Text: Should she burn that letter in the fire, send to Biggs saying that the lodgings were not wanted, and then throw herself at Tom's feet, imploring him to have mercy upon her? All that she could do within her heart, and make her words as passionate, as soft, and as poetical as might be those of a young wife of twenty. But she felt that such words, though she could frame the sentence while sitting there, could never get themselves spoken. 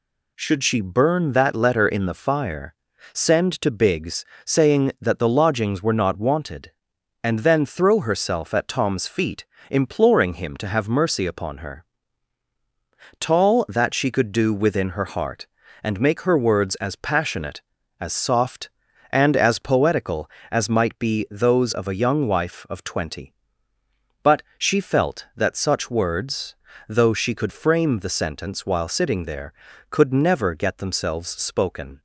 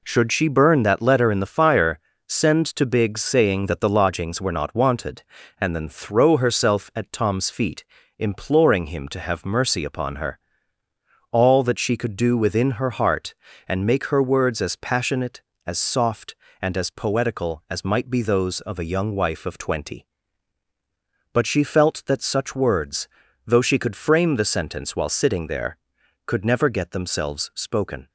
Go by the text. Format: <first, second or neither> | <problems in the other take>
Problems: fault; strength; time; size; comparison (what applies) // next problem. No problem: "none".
second | pauses between "Biggs" and "saying"; slight; at 4.2 s; 0.18 s long // says "Tall" for "All"; at 13.1 s // pauses between "But" and "she"; slight; at 24.4 s; 0.16 s long